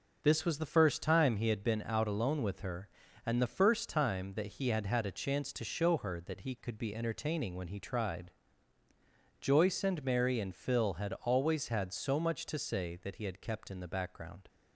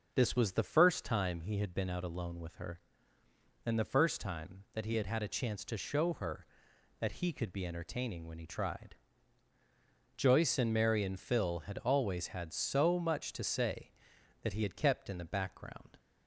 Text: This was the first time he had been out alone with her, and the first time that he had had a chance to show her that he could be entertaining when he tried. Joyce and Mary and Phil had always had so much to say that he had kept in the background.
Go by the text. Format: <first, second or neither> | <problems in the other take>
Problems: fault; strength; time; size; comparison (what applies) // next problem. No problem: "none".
neither | none